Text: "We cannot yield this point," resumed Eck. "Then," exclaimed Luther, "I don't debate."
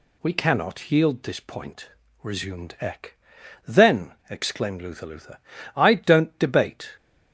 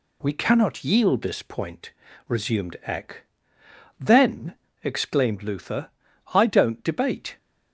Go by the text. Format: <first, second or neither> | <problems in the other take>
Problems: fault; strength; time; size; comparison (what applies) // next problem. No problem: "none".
second | says "Luther" twice; at 5.0 s